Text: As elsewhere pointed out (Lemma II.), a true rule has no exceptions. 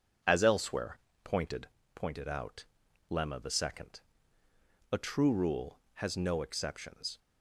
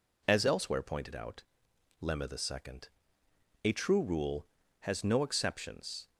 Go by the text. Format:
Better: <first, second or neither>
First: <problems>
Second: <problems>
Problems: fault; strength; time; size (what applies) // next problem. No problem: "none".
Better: second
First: pauses between "elsewhere" and "pointed"; slight; at 0.9 s; 0.26 s long // says "pointed" twice; at 1.9 s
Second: none